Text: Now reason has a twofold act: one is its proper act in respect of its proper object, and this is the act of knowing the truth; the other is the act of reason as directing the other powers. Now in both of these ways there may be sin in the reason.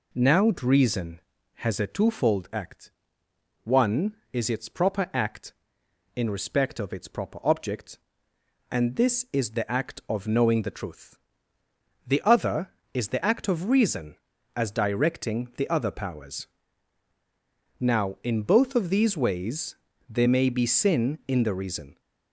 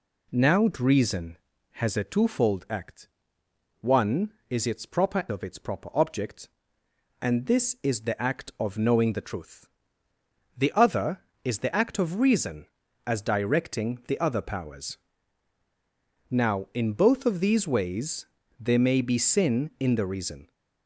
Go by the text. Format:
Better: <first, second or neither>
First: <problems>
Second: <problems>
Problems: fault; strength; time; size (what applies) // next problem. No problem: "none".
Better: first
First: pauses between "ways" and "there"; slight; at 19.7 s; 0.34 s long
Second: skips "act in respect"; at 5.2 s // pauses between "ways" and "there"; slight; at 18.2 s; 0.34 s long